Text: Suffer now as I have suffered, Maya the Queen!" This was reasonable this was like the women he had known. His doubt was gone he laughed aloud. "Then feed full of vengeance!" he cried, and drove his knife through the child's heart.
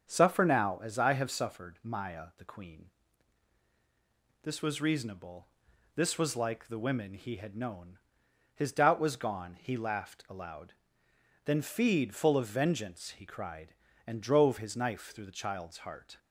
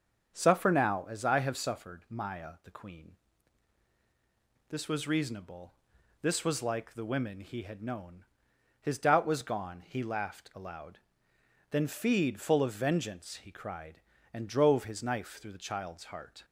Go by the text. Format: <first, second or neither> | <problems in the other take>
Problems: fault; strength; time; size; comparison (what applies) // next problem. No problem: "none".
neither | starts louder than the rest; the same in both // pauses between "reasonable" and "this"; noticeable; the same in both